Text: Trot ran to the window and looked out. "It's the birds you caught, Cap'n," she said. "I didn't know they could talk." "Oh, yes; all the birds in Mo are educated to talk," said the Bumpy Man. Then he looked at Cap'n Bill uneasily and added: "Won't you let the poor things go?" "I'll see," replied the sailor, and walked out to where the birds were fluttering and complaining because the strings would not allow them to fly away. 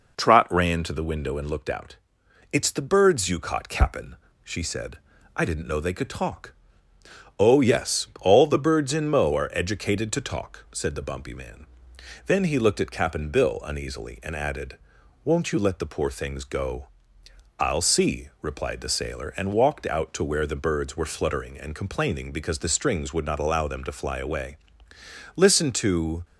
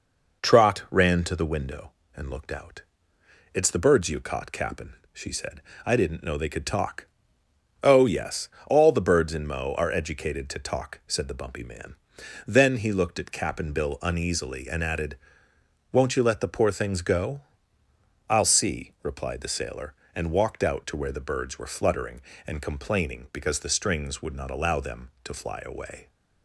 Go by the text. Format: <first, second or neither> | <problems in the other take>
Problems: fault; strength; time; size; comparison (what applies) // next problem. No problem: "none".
second | goes on to say "Listen to"; noticeable; from 25.3 s on; 0.86 s long